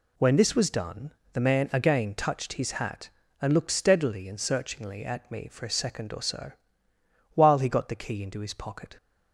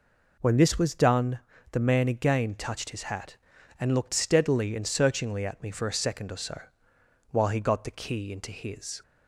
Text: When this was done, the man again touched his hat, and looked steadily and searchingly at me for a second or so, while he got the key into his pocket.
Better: first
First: none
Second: stops before "pocket"; at 9.0 s

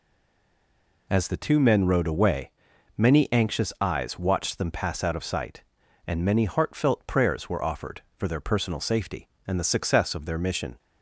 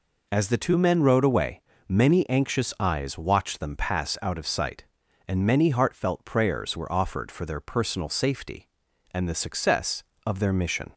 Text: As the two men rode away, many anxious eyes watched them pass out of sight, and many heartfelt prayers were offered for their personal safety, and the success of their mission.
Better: second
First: stays silent before the first word; until 1.0 s; 1.0 s long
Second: none

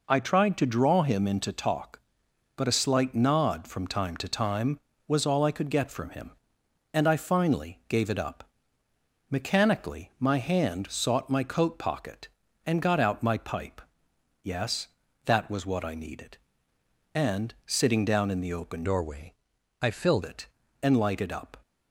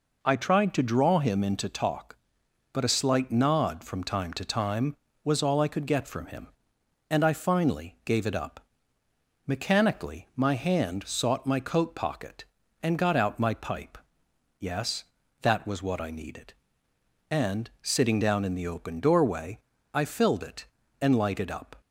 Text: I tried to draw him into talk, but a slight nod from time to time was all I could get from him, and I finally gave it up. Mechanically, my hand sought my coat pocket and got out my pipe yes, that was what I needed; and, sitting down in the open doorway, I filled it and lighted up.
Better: second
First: pauses between "pipe" and "yes"; noticeable; at 13.8 s; 0.62 s long // changes voice from "doorway" to "filled"; from 18.8 to 20.2 s; 1.4 s long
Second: pauses between "pipe" and "yes"; noticeable; at 13.9 s; 0.62 s long

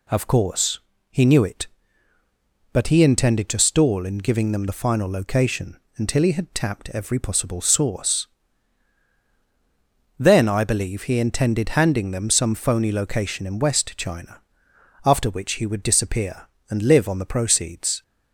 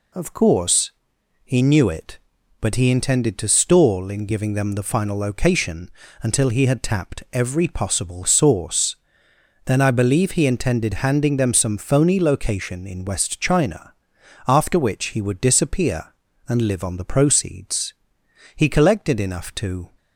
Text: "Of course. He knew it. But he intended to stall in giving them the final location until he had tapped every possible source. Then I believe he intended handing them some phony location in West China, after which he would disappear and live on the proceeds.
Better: first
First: pauses between "location" and "until"; slight; at 5.7 s; 0.18 s long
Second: pauses between "location" and "until"; slight; at 5.9 s; 0.32 s long // goes on to say "He collected enough to"; from 18.5 s on; 1.3 s long

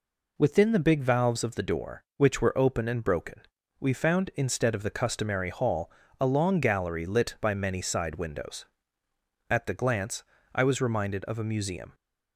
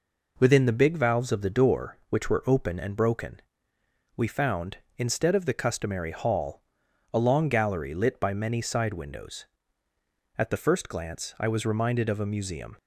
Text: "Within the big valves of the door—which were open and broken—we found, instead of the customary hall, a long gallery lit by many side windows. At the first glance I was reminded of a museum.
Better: second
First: skips "first"; at 9.7 s // pauses between "glance" and "I"; slight; at 10.2 s; 0.32 s long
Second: none

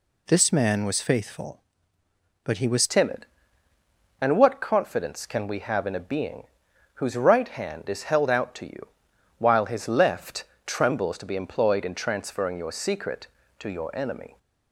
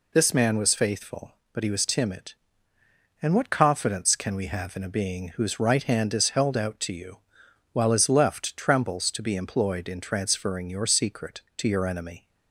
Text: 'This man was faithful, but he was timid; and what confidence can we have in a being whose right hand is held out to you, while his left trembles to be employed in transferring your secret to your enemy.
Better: second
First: changes voice at "timid"; from 2.8 s on; 11.5 s long // pauses between "being" and "whose"; noticeable; at 6.4 s; 0.50 s long // pauses between "left" and "trembles"; slight; at 10.4 s; 0.18 s long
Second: none

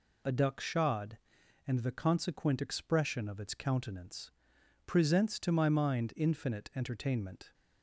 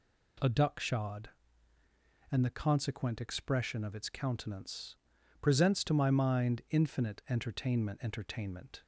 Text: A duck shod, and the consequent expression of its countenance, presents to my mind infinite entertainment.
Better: first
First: none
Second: says "entertainment" twice; at 8.0 s

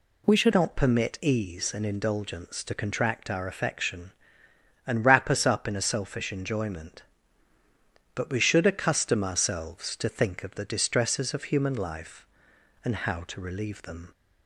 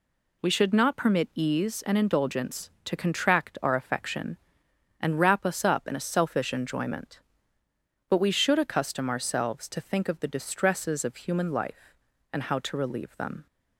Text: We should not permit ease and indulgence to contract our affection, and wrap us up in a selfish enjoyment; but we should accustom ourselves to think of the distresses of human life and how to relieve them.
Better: second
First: changes voice at "not"; from 0.5 s on; 13.6 s long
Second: none

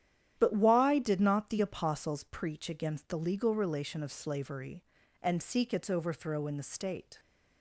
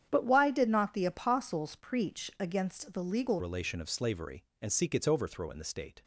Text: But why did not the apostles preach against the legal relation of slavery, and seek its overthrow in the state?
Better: first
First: starts louder than the rest; strong; until 1.3 s; 10 dB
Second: starts louder than the rest; strong; until 1.1 s; 9 dB // changes voice at "relation"; from 3.3 s on; 2.7 s long

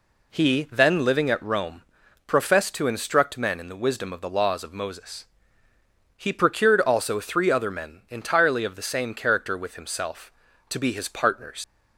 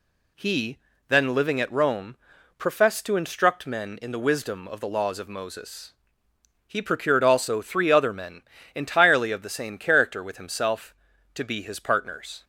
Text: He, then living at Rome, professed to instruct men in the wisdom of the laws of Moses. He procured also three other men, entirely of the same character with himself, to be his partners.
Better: second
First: leaves "partners" unfinished; at 11.6 s; 70 ms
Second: none

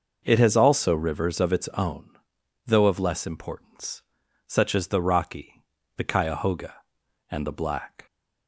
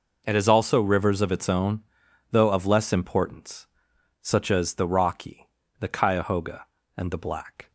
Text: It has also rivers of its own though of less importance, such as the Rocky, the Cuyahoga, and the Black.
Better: neither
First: pauses between "own" and "though"; noticeable; at 2.0 s; 0.56 s long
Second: pauses between "own" and "though"; noticeable; at 1.8 s; 0.50 s long

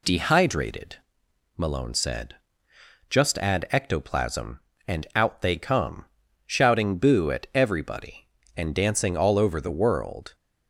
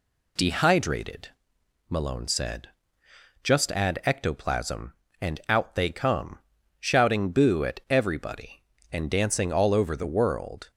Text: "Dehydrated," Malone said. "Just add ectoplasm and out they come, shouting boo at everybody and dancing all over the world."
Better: neither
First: none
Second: none

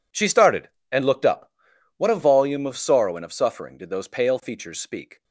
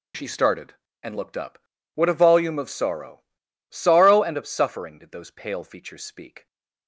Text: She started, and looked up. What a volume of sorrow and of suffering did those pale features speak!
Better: first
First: none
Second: says "sorrow" twice; at 3.6 s

